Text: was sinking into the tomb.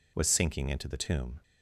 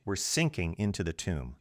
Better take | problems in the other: first | says "were" for "was"; at 0.0 s

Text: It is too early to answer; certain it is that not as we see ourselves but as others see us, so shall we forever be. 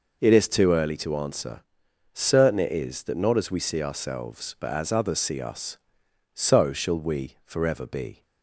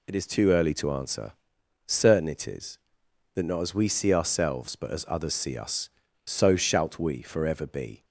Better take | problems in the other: first | says "shalt" for "shall"; at 6.5 s

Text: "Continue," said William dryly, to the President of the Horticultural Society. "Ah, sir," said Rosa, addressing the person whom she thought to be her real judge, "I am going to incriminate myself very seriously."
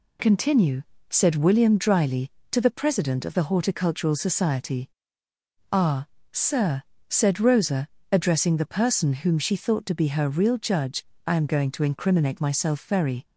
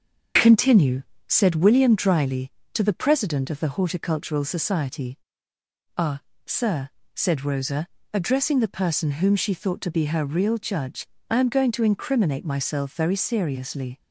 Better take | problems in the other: second | stops before "seriously"; at 13.2 s

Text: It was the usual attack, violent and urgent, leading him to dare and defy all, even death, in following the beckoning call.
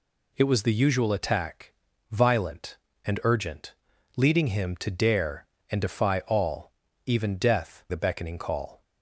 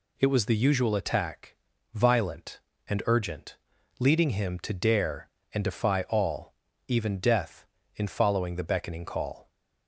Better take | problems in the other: second | skips "in following"; at 7.8 s

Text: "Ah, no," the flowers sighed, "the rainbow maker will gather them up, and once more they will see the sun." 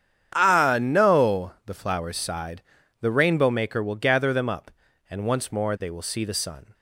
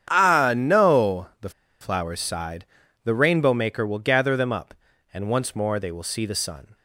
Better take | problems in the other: first | starts louder than the rest; strong; until 1.1 s; 9 dB; strong in the first // pauses between "the" and "flowers"; slight; at 1.5 s; 0.30 s long

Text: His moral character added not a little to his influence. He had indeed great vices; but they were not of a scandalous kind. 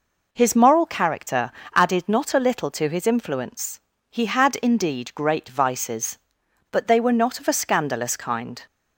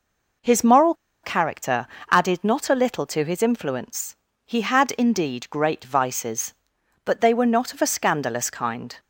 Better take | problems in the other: first | pauses between "moral" and "character"; slight; at 0.9 s; 0.30 s long // pauses between "character" and "added"; slight; at 1.8 s; 0.24 s long; slight in the first

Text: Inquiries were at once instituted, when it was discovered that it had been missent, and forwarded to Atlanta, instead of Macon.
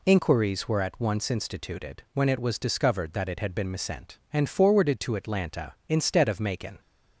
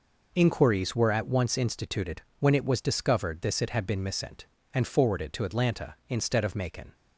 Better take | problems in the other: first | says "this" for "that"; at 3.4 s

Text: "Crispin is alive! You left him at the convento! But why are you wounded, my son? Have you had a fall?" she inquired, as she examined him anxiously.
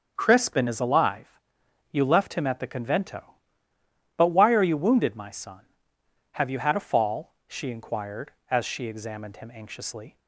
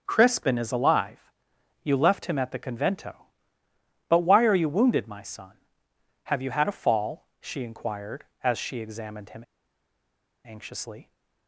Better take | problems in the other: first | starts louder than the rest; until 1.0 s; 6.5 dB; also in the first // pauses between "him" and "anxiously"; at 9.4 s; 1.0 s long

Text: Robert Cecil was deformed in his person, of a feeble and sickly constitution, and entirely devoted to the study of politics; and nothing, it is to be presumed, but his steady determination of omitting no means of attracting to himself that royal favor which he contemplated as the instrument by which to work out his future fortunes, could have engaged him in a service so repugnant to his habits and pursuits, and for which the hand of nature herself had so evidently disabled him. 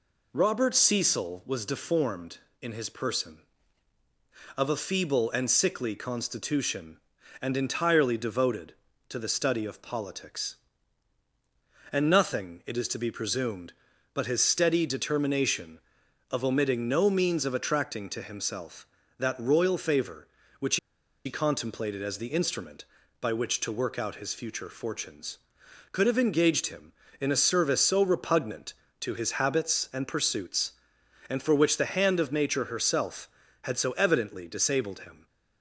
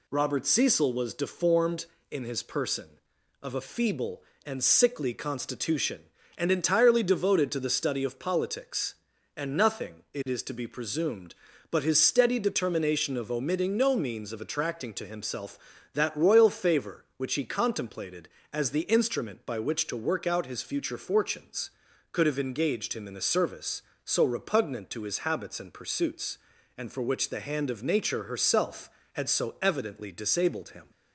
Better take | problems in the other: second | pauses between "which" and "he"; noticeable; at 20.7 s; 0.49 s long

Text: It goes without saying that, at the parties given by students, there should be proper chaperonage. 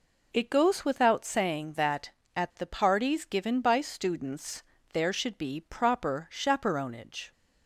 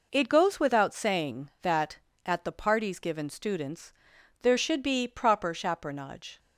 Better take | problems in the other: first | skips "by"; at 3.2 s

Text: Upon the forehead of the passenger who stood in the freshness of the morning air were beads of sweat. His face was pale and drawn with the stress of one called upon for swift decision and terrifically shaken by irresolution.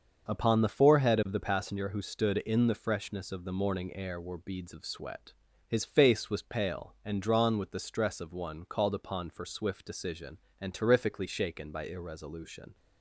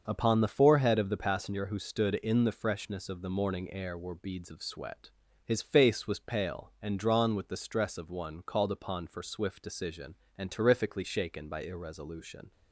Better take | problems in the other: neither | starts louder than the rest; the same in both

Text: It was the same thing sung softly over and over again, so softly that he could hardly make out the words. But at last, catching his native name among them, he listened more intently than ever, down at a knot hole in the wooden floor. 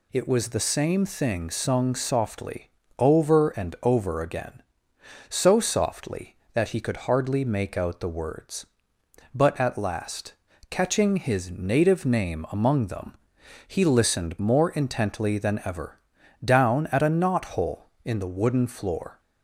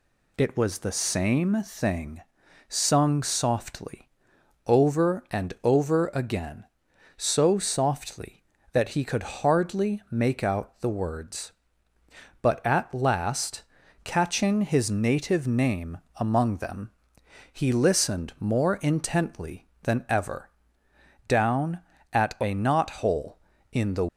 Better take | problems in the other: first | pauses between "thing" and "sung"; noticeable; at 2.2 s; 0.46 s long // pauses between "softly" and "over"; noticeable; at 4.0 s; 0.58 s long; slight in the first // pauses between "name" and "among"; slight; at 15.9 s; 0.18 s long // stops before "wooden floor"; at 24.0 s

